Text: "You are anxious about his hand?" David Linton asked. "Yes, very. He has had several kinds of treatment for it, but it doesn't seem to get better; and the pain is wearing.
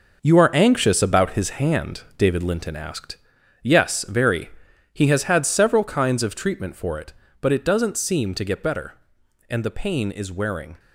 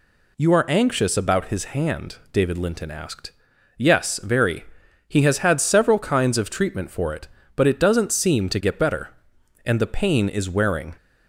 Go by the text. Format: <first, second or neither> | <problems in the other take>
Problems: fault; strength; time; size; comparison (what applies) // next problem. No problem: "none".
second | gets quieter; strong; throughout; 8.5 dB